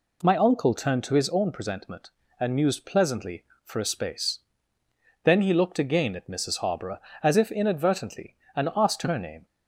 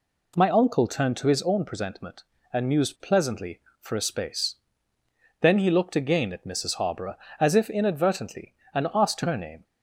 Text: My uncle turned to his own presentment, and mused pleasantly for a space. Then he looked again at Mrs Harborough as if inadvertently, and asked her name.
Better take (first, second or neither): neither